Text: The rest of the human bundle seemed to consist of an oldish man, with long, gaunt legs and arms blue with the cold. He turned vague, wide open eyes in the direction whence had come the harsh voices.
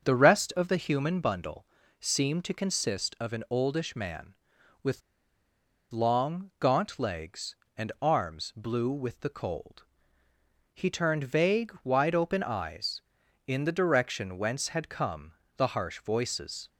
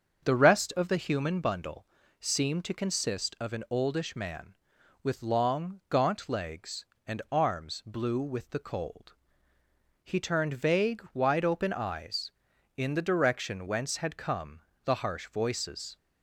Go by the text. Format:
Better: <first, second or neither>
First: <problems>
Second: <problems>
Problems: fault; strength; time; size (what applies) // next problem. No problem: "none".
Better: second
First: starts louder than the rest; until 1.1 s; 7 dB // pauses between "bundle" and "seemed"; slight; at 1.6 s; 0.36 s long // pauses between "with" and "long"; noticeable; at 5.0 s; 0.90 s long // pauses between "come" and "the"; slight; at 15.3 s; 0.24 s long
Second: starts louder than the rest; until 1.3 s; 7 dB // pauses between "bundle" and "seemed"; slight; at 1.8 s; 0.36 s long // pauses between "come" and "the"; slight; at 14.6 s; 0.24 s long